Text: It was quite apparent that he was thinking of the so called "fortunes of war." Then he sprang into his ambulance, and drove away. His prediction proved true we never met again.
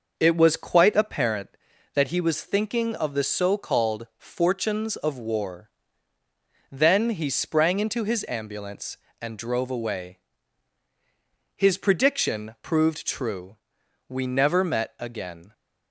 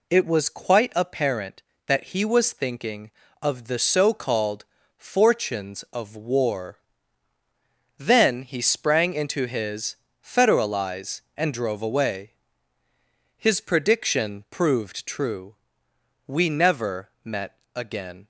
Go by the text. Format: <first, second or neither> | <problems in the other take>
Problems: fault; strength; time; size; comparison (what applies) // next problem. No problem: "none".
first | pauses between "called" and "fortunes"; slight; at 4.6 s; 0.34 s long // says "federalize" for "ambulance"; at 10.2 s // pauses between "true" and "we"; noticeable; at 15.5 s; 0.72 s long; noticeable in the first // pauses between "met" and "again"; slight; at 17.5 s; 0.18 s long